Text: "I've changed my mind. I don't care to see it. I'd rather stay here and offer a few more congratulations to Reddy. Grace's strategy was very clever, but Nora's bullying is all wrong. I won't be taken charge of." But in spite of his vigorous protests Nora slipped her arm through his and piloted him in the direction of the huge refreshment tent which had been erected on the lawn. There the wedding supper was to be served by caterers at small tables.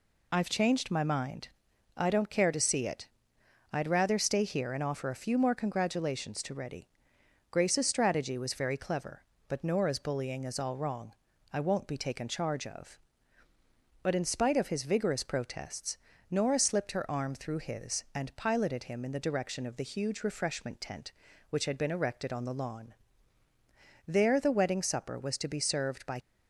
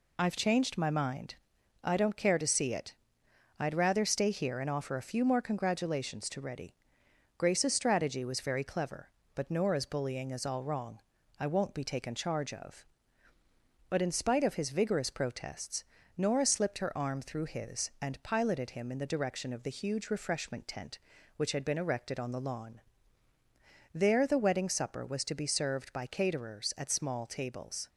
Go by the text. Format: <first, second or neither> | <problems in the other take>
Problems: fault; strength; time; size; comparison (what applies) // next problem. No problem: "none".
second | pauses between "protests" and "Nora"; slight; at 15.9 s; 0.32 s long; slight in the second // stops before "caterers at small tables"; at 26.2 s